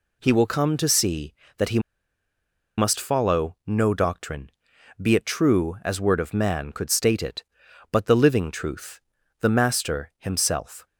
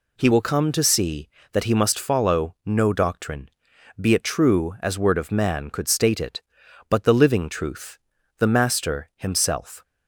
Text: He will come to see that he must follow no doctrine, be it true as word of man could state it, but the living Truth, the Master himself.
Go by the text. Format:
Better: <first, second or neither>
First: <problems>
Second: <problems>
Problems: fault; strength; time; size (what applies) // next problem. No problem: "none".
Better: second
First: pauses between "he" and "must"; at 1.7 s; 0.98 s long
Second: none